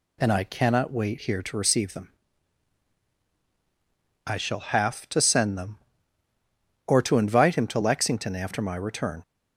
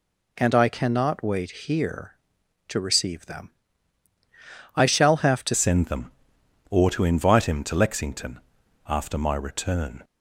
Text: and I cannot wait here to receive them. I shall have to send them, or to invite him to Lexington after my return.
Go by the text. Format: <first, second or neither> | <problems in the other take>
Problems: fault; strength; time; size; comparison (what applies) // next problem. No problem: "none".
first | changes voice at "send"; from 5.5 s on; 4.5 s long // pauses between "Lexington" and "after"; noticeable; at 8.3 s; 0.48 s long